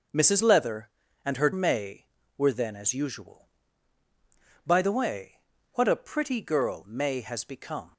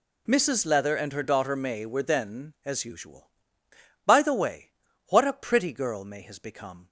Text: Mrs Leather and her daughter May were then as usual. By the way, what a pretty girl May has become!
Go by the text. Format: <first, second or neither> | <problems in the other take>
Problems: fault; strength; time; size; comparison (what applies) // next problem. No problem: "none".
second | skips "daughter"; at 1.5 s